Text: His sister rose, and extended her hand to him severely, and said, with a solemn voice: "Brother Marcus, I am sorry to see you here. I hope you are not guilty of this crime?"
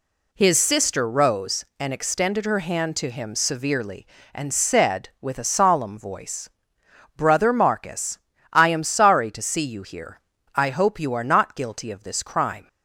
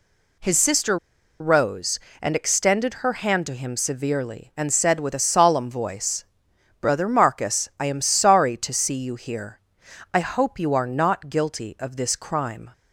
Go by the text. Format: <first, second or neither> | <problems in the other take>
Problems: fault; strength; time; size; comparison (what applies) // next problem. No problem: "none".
first | pauses between "sister" and "rose"; at 0.9 s; 0.43 s long